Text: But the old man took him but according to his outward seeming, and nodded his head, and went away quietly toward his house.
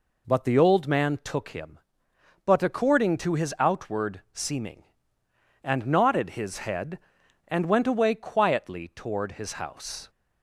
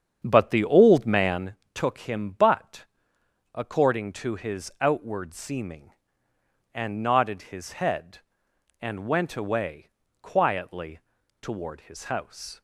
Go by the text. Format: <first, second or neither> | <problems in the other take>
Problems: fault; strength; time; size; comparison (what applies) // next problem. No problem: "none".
first | starts louder than the rest; strong; until 1.4 s; 8 dB // pauses between "man" and "took"; slight; at 1.5 s; 0.18 s long // pauses between "but" and "according"; noticeable; at 2.8 s; 0.70 s long // pauses between "away" and "quietly"; slight; at 9.8 s; 0.32 s long // pauses between "quietly" and "toward"; at 10.9 s; 0.42 s long